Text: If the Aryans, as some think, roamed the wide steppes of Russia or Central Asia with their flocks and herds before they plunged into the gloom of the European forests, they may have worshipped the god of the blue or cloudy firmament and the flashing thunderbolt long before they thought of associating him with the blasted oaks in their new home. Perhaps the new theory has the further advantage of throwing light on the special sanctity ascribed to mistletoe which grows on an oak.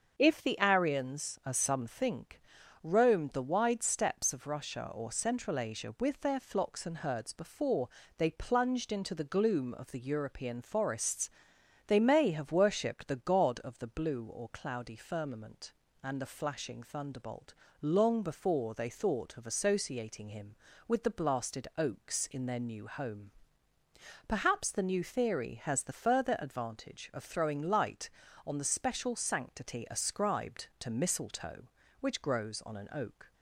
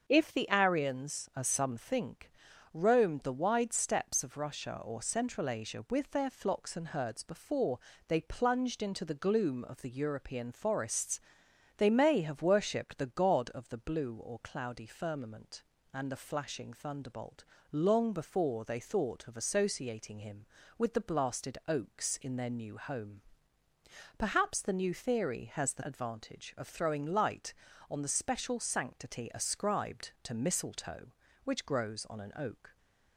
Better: first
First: starts louder than the rest; until 1.2 s; 6.5 dB // pauses between "before" and "they"; slight; at 7.8 s; 0.30 s long // pauses between "thunderbolt" and "long"; slight; at 17.5 s; 0.30 s long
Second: starts louder than the rest; until 1.1 s; 6.5 dB // pauses between "before" and "they"; slight; at 7.7 s; 0.30 s long // pauses between "thunderbolt" and "long"; slight; at 17.4 s; 0.30 s long // skips "further"; at 25.8 s

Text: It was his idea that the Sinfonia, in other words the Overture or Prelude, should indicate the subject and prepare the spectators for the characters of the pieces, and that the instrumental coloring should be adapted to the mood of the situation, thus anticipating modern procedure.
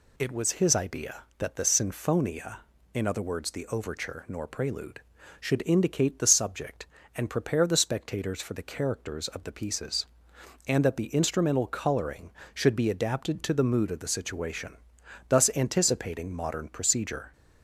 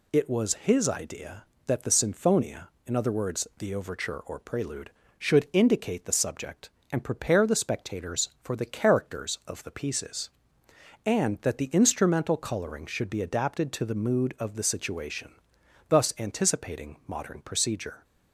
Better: second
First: says "nor" for "or"; at 4.2 s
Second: none

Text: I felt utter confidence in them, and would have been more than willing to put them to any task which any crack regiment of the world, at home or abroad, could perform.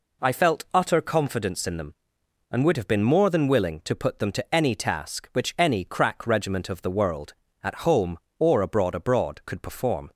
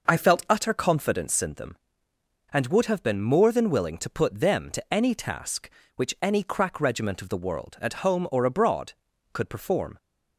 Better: second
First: says "abroad" twice; at 8.9 s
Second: none

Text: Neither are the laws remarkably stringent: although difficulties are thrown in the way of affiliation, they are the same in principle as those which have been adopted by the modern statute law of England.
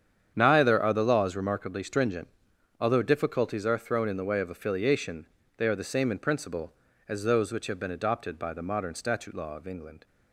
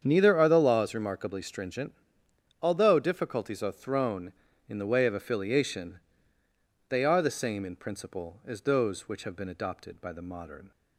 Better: first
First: starts louder than the rest; strong; until 1.3 s; 8.5 dB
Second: starts louder than the rest; strong; until 1.0 s; 7.5 dB // stops before "statute law of England"; at 10.7 s

